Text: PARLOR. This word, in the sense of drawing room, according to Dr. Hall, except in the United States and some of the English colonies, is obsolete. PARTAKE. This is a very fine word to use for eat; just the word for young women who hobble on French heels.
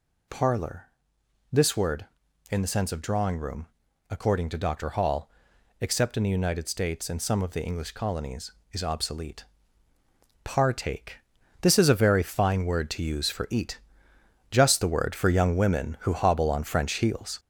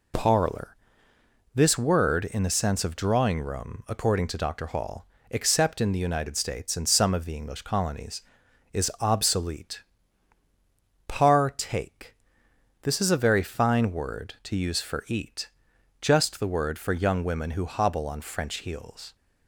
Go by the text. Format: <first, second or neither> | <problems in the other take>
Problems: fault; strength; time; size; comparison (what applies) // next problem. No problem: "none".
second | gets louder; noticeable; throughout; 5 dB